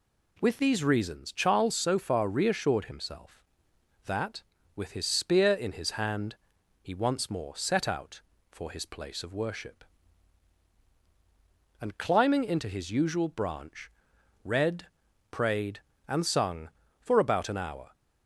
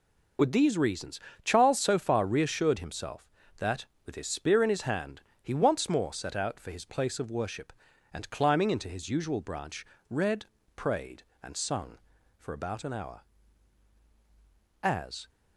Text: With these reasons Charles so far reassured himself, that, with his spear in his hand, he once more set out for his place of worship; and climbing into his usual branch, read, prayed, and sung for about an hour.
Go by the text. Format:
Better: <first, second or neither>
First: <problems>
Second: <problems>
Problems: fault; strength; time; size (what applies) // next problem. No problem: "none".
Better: first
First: none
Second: pauses between "reasons" and "Charles"; slight; at 1.2 s; 0.24 s long // goes on to say "As"; slight; from 14.8 s on; 0.46 s long